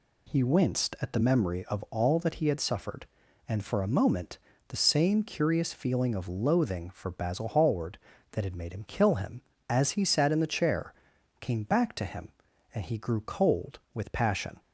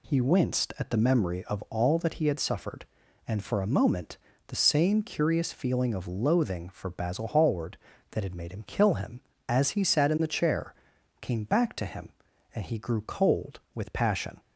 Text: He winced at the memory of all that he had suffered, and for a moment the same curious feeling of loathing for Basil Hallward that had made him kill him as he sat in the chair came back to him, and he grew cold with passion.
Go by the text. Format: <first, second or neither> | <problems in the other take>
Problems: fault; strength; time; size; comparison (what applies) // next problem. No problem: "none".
neither | pauses between "moment" and "the"; slight; the same in both // pauses between "chair" and "came"; noticeable; the same in both